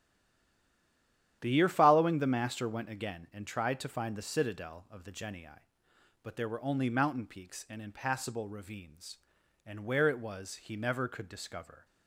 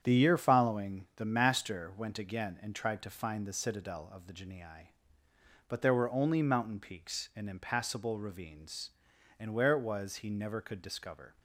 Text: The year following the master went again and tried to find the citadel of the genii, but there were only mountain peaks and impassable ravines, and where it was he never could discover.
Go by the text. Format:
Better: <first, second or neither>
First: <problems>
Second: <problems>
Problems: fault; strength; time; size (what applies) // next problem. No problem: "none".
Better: second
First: stays silent before the first word; noticeable; until 1.4 s; 1.4 s long // starts louder than the rest; strong; until 2.4 s; 10.5 dB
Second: starts louder than the rest; strong; until 1.0 s; 8 dB